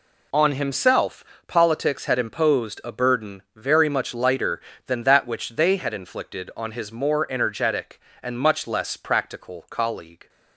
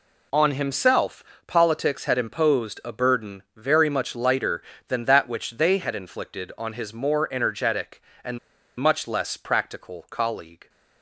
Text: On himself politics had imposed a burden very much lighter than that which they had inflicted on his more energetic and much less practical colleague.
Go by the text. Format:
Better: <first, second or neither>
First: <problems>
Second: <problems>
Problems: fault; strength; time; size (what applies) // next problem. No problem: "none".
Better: first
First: pauses between "himself" and "politics"; slight; at 1.2 s; 0.22 s long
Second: pauses between "himself" and "politics"; slight; at 1.2 s; 0.22 s long // pauses between "and" and "much"; at 8.3 s; 0.39 s long